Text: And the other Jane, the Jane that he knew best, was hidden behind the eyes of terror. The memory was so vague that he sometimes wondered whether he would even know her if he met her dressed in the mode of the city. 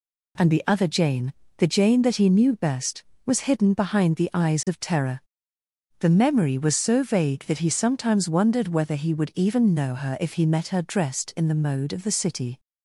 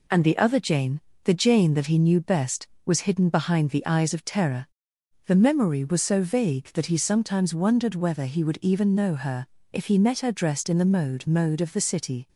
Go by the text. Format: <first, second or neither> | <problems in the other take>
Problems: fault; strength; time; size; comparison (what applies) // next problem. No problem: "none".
first | pauses between "her" and "if"; slight; at 9.4 s; 0.26 s long // says "mode" twice; at 11.2 s